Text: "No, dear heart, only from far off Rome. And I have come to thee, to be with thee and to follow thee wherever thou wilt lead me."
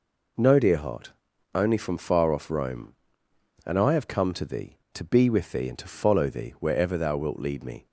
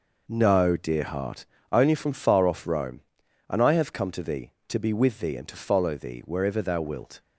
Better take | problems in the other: first | stops before "lead me"; at 7.1 s

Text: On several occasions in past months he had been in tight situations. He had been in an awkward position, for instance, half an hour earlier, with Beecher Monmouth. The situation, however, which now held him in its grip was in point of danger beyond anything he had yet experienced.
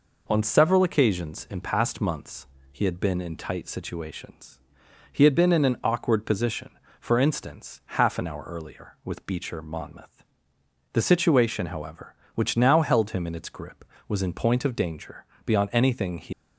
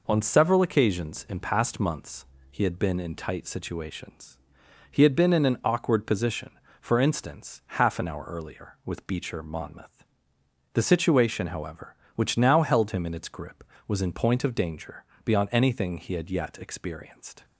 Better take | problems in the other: second | pauses between "months" and "he"; slight; at 2.4 s; 0.24 s long; slight in the second // pauses between "danger" and "beyond"; slight; at 15.2 s; 0.18 s long; slight in the second // stops before "had yet experienced"; at 16.3 s

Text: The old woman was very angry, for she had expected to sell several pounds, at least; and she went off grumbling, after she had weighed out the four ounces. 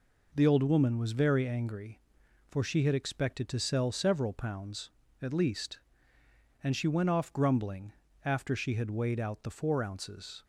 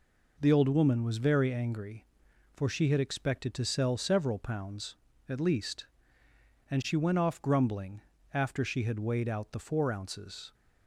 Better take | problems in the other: neither | none

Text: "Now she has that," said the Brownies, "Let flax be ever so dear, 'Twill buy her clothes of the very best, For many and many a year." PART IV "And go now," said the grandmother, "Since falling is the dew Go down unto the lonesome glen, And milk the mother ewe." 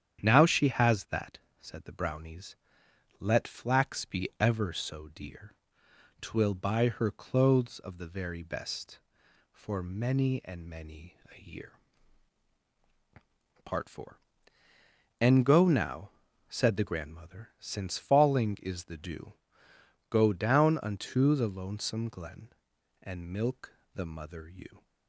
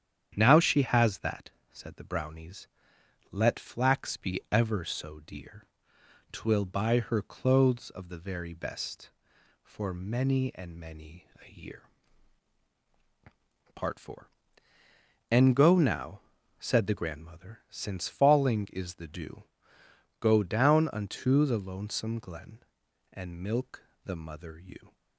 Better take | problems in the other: neither | starts louder than the rest; strong; the same in both // pauses between "dew" and "Go"; noticeable; the same in both // pauses between "milk" and "the"; slight; the same in both

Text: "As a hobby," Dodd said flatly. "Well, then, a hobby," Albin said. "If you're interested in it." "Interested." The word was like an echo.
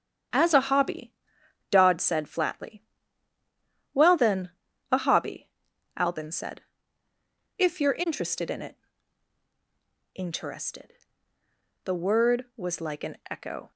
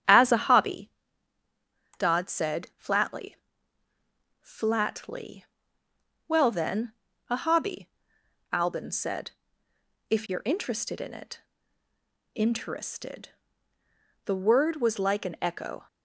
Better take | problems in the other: first | starts louder than the rest; strong; until 2.1 s; 9 dB; strong in the first // says "flatly" twice; at 4.3 s

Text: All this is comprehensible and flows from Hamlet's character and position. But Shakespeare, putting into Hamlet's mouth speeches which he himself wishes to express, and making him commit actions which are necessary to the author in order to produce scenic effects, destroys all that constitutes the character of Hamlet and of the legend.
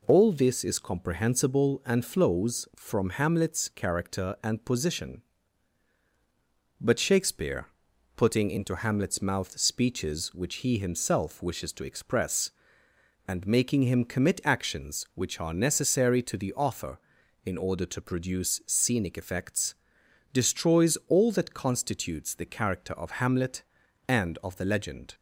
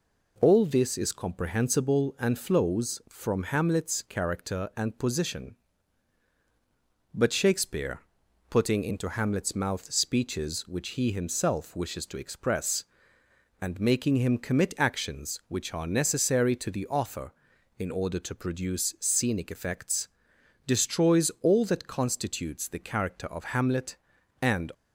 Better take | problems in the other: first | stops before "of the legend"; at 24.7 s

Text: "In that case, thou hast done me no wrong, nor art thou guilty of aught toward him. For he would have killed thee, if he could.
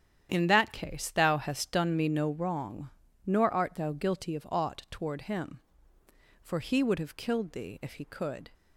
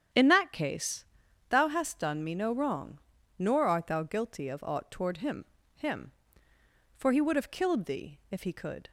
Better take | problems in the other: first | starts louder than the rest; strong; until 1.5 s; 8.5 dB; strong in the first // says "him" twice; at 5.7 s

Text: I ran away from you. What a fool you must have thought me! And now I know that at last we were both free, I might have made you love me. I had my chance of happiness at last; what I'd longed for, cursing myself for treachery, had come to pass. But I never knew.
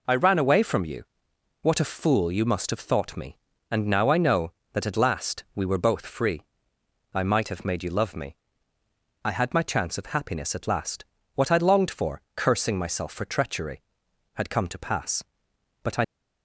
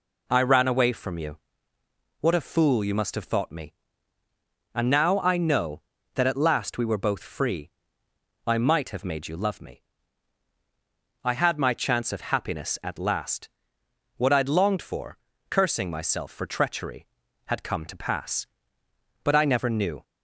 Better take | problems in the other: second | stops before "never knew"; at 16.0 s

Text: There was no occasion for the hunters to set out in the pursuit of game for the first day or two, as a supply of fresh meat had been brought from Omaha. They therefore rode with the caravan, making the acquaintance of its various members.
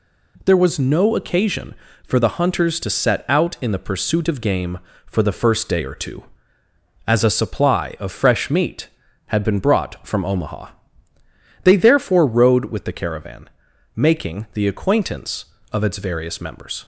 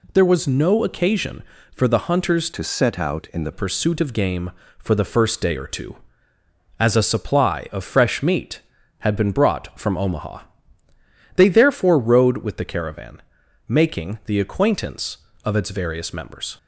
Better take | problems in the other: first | changes voice from "to" to "the"; from 2.5 to 3.5 s; 1.0 s long

